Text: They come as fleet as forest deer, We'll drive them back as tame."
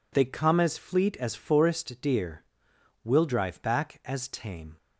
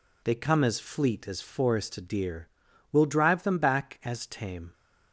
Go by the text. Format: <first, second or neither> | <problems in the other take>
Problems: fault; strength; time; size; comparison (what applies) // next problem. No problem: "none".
second | skips "them"; at 3.6 s